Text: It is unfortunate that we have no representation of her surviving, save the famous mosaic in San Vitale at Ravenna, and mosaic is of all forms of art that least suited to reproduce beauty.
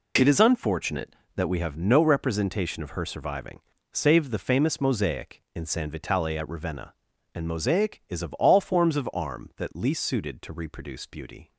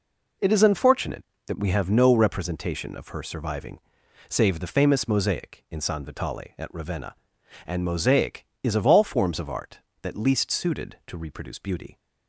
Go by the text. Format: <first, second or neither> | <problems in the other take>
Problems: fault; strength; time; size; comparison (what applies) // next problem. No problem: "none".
second | says "arm" for "art"; at 9.1 s